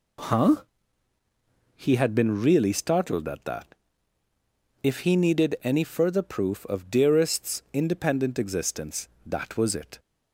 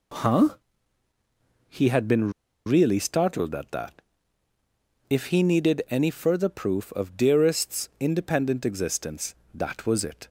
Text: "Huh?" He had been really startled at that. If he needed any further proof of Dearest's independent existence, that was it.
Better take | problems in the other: first | pauses between "been" and "really"; slight; at 2.3 s; 0.35 s long

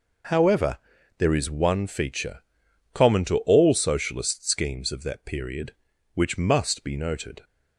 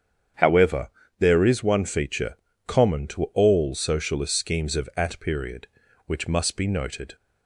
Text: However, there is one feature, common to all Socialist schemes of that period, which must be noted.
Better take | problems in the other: first | starts louder than the rest; strong; until 1.6 s; 8 dB // says "at" for "that"; at 4.9 s

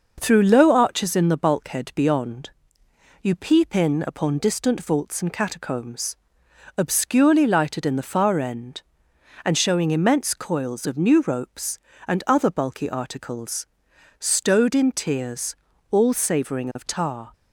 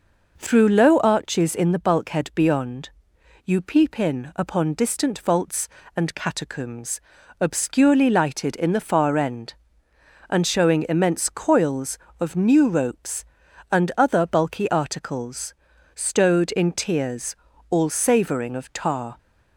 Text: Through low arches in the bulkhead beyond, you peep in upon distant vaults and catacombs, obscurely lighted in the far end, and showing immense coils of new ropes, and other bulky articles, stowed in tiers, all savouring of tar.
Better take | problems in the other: neither | none

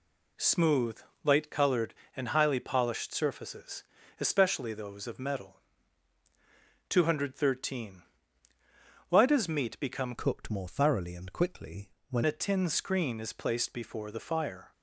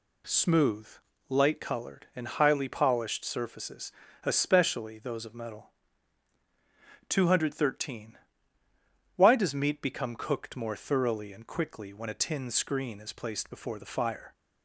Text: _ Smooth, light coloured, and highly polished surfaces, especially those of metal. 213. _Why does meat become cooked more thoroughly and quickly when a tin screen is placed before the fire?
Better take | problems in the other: second | changes voice from "cooked" to "when"; from 10.1 to 12.2 s; 2.1 s long // pauses between "quickly" and "when"; slight; at 11.8 s; 0.20 s long

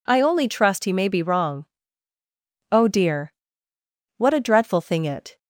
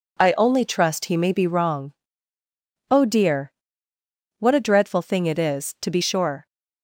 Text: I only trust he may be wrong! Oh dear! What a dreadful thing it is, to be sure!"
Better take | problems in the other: second | stops before "is to be sure"; at 5.3 s

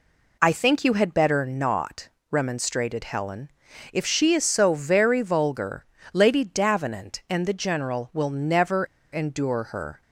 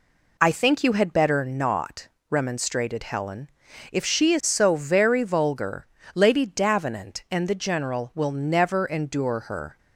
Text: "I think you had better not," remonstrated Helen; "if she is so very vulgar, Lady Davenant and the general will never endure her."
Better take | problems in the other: second | pauses between "never" and "endure"; slight; at 8.8 s; 0.28 s long

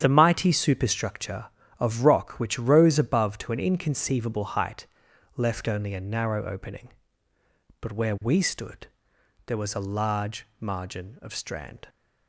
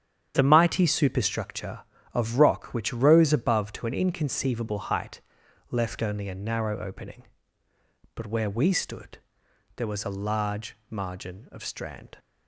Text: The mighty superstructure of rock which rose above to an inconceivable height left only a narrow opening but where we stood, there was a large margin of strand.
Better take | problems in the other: neither | starts louder than the rest; strong; the same in both // pauses between "height" and "left"; noticeable; the same in both // pauses between "large" and "margin"; slight; the same in both

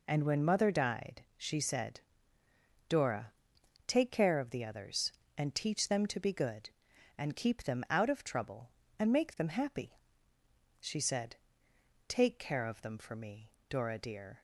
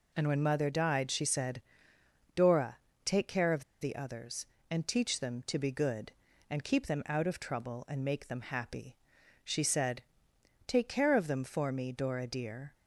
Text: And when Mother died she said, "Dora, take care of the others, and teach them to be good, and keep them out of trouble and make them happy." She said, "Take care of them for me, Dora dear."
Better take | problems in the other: first | pauses between "of" and "the"; slight; at 3.6 s; 0.18 s long

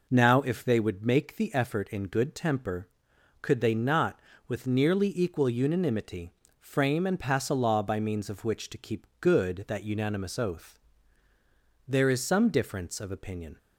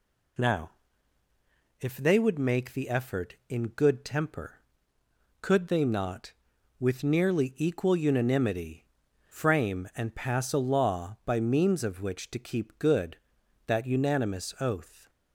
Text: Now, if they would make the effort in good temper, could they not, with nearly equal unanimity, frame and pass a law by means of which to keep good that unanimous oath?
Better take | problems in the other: second | goes on to say "There is some difference of opinion"; strong; from 11.8 s on; 1.7 s long

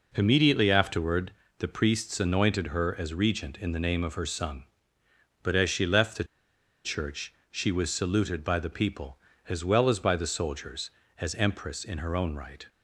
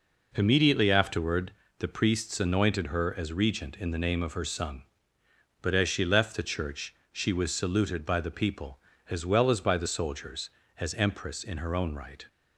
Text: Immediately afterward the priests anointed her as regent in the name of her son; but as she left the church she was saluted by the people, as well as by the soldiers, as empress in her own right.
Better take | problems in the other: second | pauses between "afterward" and "the"; slight; at 1.3 s; 0.24 s long; slight in the second // pauses between "the" and "church"; noticeable; at 6.2 s; 0.60 s long // pauses between "church" and "she"; slight; at 7.3 s; 0.16 s long; slight in the second

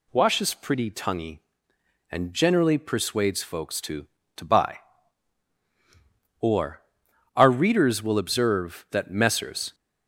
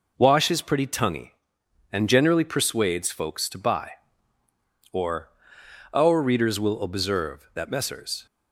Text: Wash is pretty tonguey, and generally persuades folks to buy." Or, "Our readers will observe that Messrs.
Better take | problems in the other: second | says "to" twice; at 4.3 s

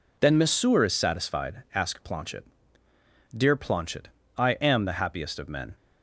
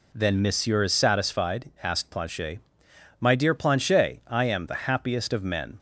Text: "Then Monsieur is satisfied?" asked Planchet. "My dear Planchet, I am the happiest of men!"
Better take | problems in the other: second | skips "My"; at 2.8 s

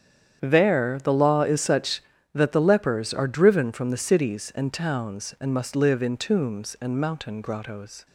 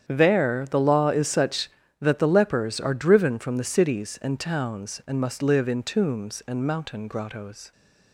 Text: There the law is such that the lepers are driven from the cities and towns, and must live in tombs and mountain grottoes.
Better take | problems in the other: neither | starts louder than the rest; strong; the same in both

